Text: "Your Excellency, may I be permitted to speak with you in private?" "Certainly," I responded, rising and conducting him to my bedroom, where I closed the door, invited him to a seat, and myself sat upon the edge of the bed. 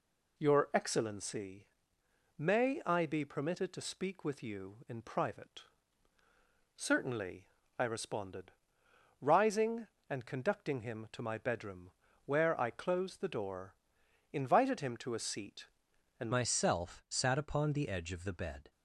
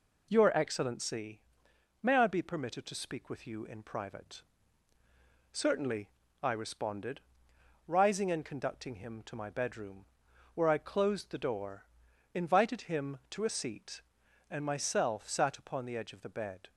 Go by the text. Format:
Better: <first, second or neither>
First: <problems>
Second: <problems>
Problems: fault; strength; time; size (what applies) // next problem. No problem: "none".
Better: second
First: changes voice at "myself"; from 16.3 s on; 2.4 s long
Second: none